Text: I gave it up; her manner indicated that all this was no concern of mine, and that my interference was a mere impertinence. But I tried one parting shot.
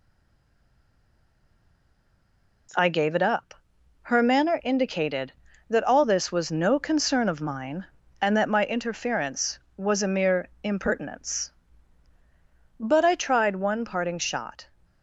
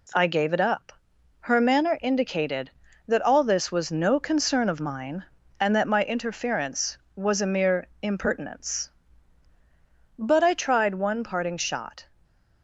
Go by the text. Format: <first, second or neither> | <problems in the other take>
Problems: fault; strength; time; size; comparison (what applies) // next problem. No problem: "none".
second | stays silent before the first word; strong; until 2.6 s; 2.6 s long